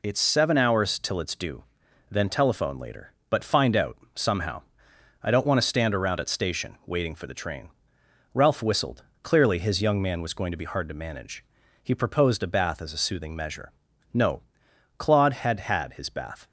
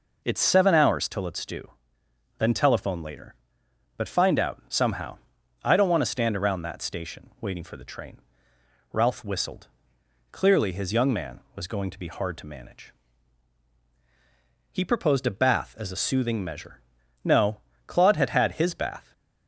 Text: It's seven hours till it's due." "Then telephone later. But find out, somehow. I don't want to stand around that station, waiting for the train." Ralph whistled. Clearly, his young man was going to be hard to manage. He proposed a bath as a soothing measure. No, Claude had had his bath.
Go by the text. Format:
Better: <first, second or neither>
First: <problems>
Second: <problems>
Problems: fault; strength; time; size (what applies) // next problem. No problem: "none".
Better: second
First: says "at" for "that"; at 6.1 s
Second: none